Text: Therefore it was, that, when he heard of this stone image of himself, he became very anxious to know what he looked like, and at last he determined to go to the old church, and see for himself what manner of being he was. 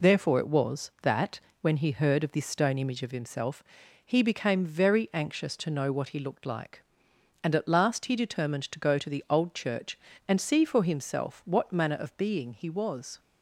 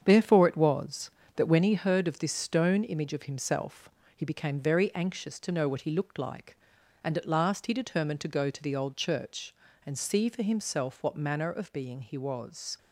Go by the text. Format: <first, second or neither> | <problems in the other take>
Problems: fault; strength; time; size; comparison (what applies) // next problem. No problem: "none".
first | gets quieter; strong; throughout; 7.5 dB